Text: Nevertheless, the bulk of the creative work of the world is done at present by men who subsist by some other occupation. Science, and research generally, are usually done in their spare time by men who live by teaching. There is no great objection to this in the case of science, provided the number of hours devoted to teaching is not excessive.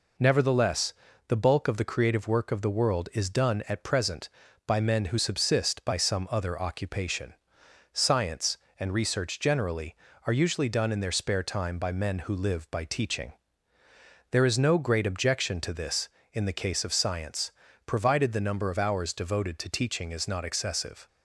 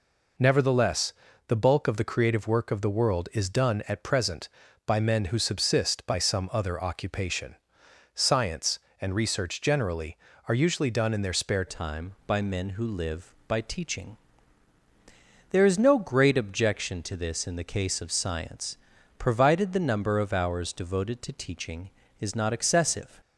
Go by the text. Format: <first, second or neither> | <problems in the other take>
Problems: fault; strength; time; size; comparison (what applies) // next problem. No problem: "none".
first | changes voice at "time"; from 11.6 s on; 11.6 s long